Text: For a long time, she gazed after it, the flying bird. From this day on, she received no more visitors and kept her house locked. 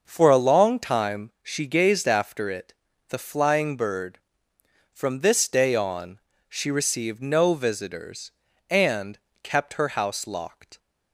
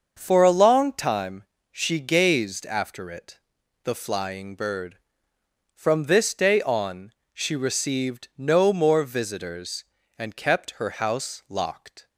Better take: second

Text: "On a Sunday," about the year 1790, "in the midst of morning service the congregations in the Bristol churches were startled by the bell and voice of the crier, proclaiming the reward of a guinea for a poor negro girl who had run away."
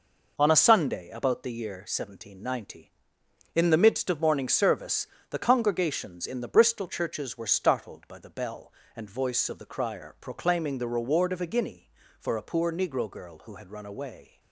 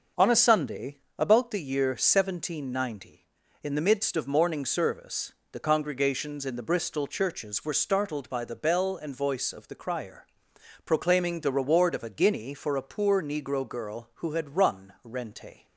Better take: first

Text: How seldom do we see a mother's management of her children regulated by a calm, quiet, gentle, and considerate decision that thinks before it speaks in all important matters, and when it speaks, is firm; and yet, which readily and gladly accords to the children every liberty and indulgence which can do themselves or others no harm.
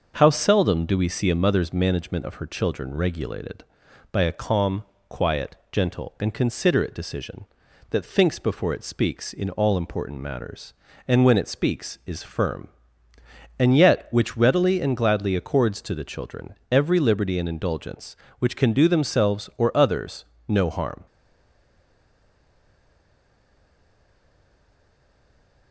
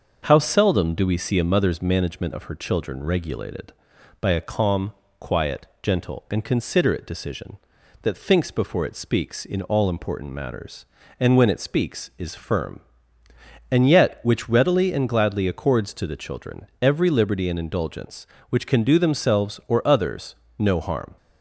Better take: second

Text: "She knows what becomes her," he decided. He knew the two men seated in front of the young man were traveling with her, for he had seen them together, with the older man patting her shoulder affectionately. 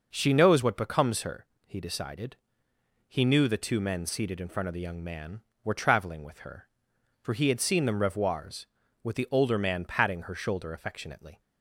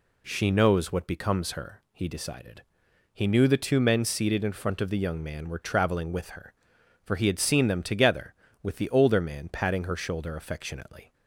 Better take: second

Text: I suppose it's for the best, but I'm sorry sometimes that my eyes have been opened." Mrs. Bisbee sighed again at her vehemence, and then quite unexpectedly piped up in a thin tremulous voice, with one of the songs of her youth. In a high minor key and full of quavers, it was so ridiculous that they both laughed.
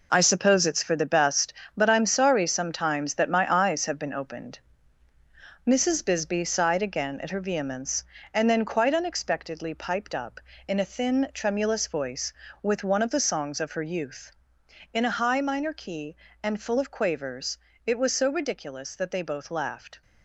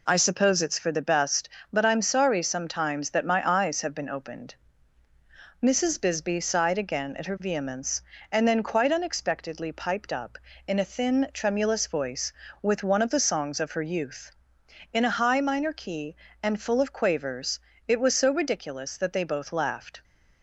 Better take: second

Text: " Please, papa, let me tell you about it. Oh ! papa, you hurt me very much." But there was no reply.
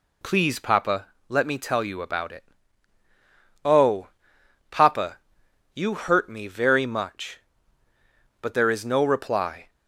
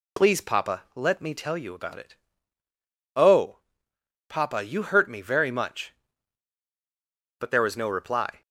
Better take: second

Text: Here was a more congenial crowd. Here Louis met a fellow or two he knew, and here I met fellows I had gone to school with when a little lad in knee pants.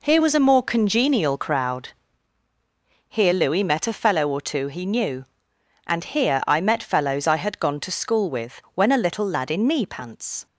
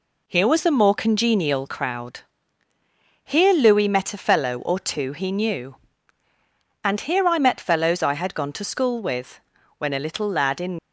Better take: first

